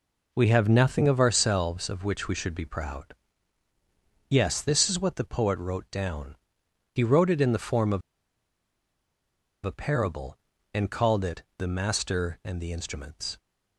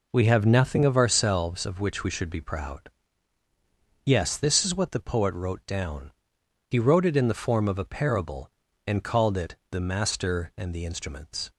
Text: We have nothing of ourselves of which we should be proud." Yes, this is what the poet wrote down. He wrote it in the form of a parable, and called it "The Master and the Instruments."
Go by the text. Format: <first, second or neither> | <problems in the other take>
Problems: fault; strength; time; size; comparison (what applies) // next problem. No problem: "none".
second | pauses between "of" and "a"; strong; at 8.0 s; 1.6 s long